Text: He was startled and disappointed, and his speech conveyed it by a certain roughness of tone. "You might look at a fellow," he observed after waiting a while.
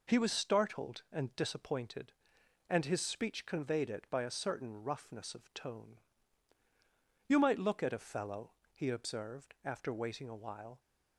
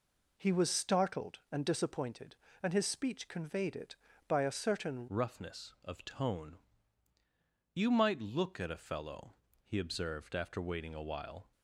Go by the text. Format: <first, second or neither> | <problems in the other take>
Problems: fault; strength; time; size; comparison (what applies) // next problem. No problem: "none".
first | changes voice at "roughness"; from 5.0 s on; 6.5 s long